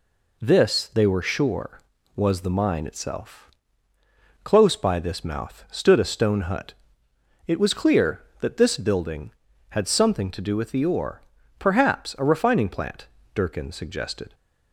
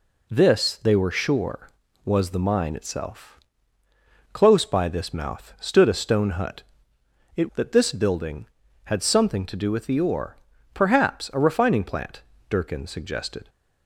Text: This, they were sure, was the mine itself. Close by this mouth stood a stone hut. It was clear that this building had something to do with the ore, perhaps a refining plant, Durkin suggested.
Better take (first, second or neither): first